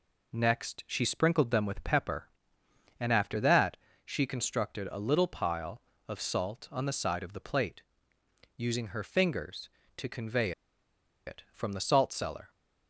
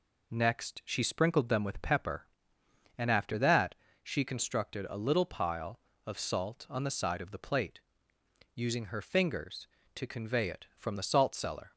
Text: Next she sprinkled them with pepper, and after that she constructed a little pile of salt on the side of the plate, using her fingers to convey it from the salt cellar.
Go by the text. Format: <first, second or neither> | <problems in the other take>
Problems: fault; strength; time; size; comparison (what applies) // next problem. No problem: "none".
second | pauses between "that" and "she"; slight; at 3.7 s; 0.26 s long; slight in the second // pauses between "convey" and "it"; noticeable; at 10.5 s; 0.75 s long